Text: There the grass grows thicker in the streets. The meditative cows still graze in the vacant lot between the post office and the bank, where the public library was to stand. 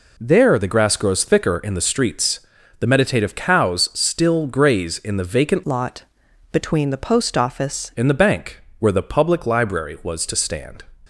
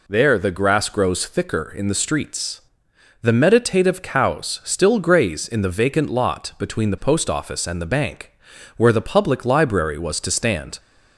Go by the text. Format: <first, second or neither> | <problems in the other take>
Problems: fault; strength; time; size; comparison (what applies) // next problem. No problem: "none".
second | changes voice from "lot" to "office"; from 5.6 to 7.8 s; 2.2 s long // pauses between "lot" and "between"; noticeable; at 6.0 s; 0.48 s long